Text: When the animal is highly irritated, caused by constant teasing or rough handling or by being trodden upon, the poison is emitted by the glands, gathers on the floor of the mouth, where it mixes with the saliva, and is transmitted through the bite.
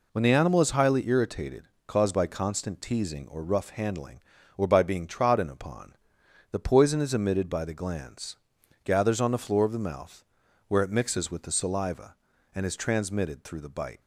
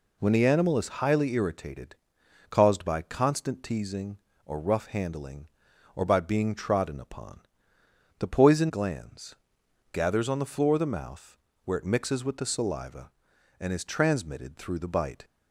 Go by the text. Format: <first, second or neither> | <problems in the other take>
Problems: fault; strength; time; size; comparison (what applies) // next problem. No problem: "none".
first | skips "is emitted by the"; at 8.6 s